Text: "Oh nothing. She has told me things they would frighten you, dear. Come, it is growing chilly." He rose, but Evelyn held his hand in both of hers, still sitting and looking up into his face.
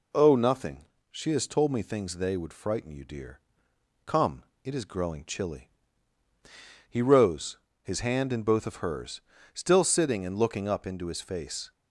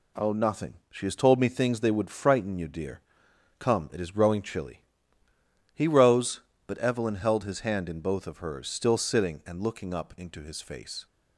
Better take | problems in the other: second | skips "but Evelyn held"; at 7.6 s

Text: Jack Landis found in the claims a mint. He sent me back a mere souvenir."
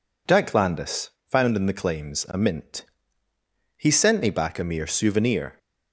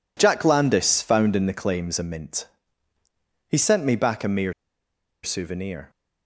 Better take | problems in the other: first | pauses between "mere" and "souvenir"; noticeable; at 4.5 s; 0.70 s long

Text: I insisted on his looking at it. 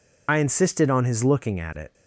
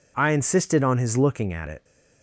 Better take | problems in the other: second | loses the start of "I"; at 0.2 s; 70 ms

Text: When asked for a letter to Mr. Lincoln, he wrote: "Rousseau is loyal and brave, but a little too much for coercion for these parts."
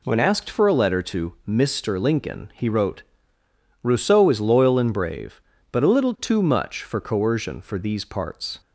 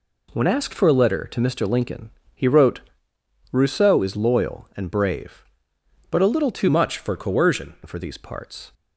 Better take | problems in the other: first | changes voice from "much" to "coercion"; from 6.6 to 7.7 s; 1.1 s long

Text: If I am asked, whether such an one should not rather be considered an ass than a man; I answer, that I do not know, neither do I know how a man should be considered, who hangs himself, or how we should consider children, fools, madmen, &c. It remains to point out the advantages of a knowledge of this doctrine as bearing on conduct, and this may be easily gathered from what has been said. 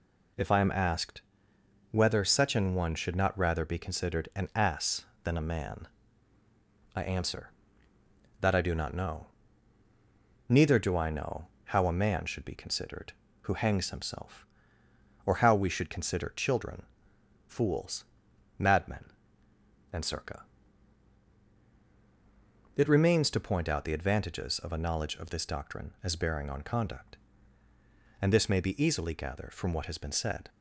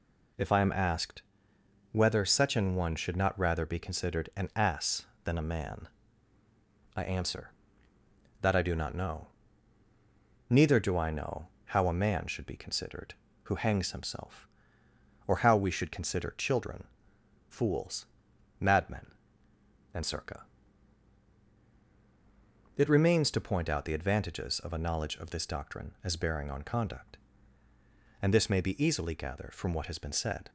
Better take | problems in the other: neither | pauses between "know" and "how"; slight; the same in both

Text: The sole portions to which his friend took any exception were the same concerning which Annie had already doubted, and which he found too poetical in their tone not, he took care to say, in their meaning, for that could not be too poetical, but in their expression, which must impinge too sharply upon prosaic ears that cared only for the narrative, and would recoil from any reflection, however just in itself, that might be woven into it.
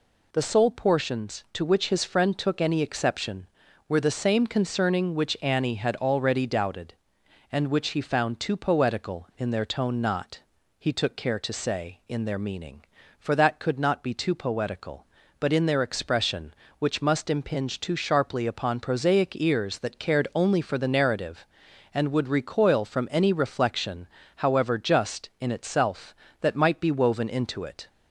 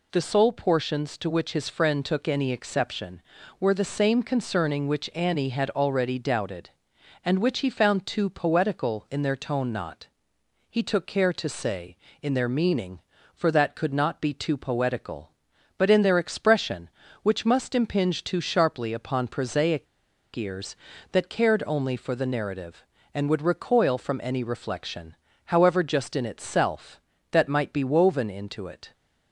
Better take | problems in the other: first | pauses between "prosaic" and "ears"; noticeable; at 19.8 s; 0.49 s long

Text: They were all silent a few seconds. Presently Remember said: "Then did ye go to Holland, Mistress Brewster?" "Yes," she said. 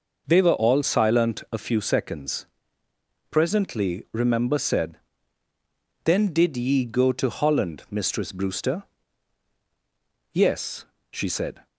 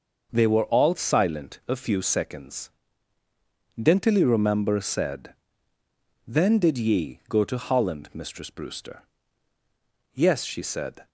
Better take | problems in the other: first | says "Dentally" for "Presently"; at 3.7 s

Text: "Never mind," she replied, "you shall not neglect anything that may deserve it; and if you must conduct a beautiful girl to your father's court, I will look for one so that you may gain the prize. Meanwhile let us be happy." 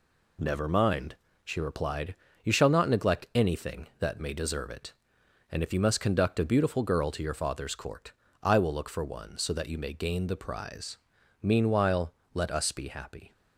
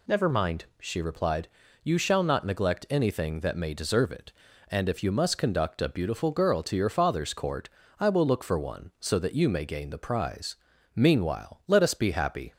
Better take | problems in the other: second | gets quieter; noticeable; throughout; 5 dB // pauses between "Meanwhile" and "let"; slight; at 12.1 s; 0.20 s long

